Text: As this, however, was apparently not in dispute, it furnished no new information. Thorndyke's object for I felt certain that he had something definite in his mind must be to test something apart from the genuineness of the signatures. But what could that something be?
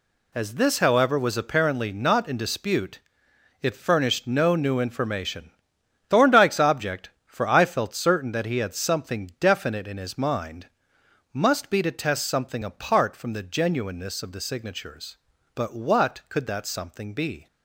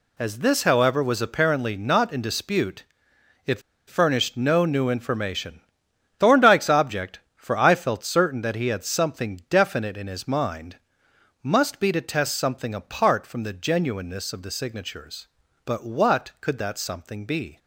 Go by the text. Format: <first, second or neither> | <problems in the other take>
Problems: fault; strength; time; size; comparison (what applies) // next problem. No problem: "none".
first | pauses between "it" and "furnished"; slight; at 3.5 s; 0.28 s long // pauses between "mind" and "must"; noticeable; at 10.7 s; 0.66 s long; noticeable in the first